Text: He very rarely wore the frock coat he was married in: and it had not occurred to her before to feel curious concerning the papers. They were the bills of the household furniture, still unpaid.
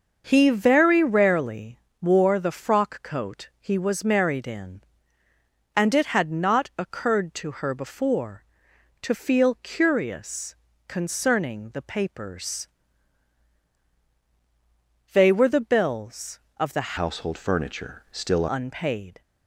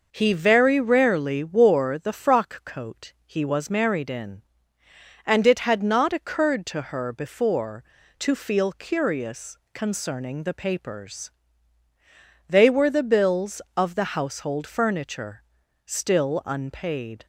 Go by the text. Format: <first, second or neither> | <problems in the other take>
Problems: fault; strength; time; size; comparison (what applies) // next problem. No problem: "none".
second | starts louder than the rest; until 1.2 s; 6.5 dB // pauses between "rarely" and "wore"; slight; at 1.7 s; 0.24 s long // pauses between "curious" and "concerning"; slight; at 10.5 s; 0.32 s long; slight in the second // changes voice from "household" to "still"; from 16.9 to 18.4 s; 1.5 s long